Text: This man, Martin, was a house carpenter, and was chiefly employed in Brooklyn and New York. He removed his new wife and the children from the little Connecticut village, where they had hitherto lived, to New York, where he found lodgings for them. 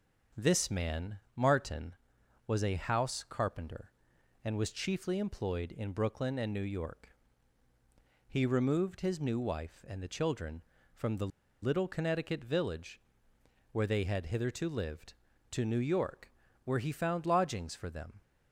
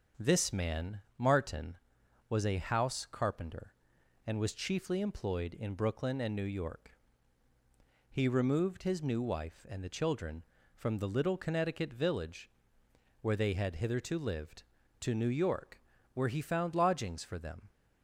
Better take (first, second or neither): second